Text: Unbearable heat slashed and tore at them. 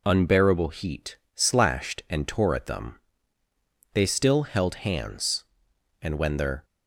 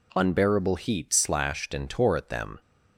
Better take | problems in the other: second | pauses between "heat" and "slashed"; slight; at 1.1 s; 0.18 s long // goes on to say "They still held hands and when their"; strong; from 3.9 s on; 2.7 s long

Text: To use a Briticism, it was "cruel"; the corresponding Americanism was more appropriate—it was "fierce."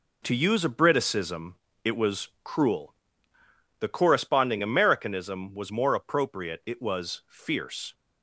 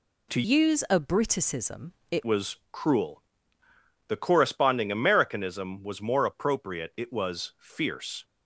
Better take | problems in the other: first | changes voice from "use" to "it"; from 0.4 to 2.2 s; 1.8 s long // pauses between "was" and "cruel"; slight; at 2.5 s; 0.16 s long; slight in the first

